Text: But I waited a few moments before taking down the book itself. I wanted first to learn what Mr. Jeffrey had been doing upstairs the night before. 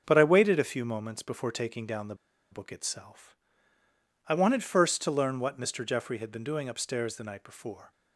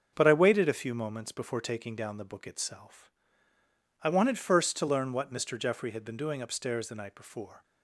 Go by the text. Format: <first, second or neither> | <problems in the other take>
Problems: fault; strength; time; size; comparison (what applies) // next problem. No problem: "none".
second | starts louder than the rest; until 1.0 s; 6 dB; noticeable in the second // pauses between "the" and "book"; at 2.1 s; 0.36 s long